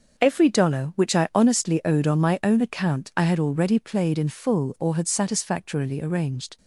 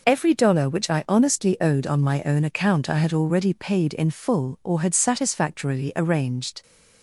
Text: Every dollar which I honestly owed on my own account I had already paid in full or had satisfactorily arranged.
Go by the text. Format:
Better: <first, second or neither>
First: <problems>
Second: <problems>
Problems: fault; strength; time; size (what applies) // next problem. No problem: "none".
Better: second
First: starts louder than the rest; until 1.2 s; 6.5 dB // says "played" for "paid"; at 3.7 s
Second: none